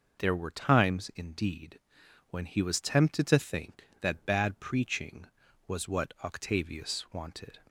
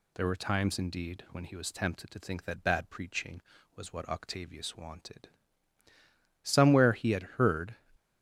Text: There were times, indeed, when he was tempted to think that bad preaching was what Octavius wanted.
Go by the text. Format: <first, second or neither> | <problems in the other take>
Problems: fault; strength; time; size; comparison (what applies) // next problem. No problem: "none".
first | goes on to say "Somewhere he had heard"; from 6.4 s on; 1.3 s long